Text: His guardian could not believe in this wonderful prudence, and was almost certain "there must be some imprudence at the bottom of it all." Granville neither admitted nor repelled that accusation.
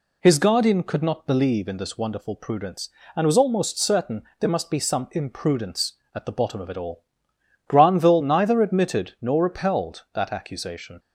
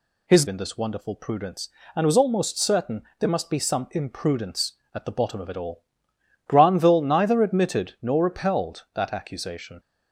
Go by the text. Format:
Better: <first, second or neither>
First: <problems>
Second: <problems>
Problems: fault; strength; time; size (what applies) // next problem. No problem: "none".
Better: first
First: pauses between "certain" and "there"; slight; at 4.2 s; 0.18 s long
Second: skips "guardian could not believe"; at 0.4 s // pauses between "certain" and "there"; slight; at 3.0 s; 0.18 s long